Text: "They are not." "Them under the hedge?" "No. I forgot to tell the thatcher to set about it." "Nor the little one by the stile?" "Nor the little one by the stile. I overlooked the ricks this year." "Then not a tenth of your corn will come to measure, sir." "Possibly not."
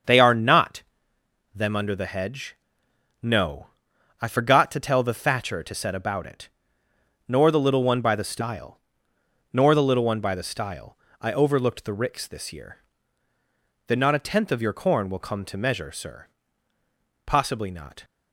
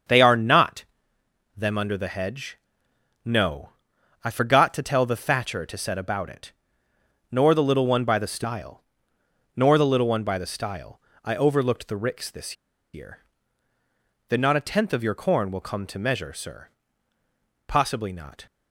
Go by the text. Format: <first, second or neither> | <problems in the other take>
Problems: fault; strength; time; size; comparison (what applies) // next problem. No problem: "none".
first | starts louder than the rest; until 1.8 s; 7 dB; also in the first // pauses between "this" and "year"; at 12.5 s; 0.38 s long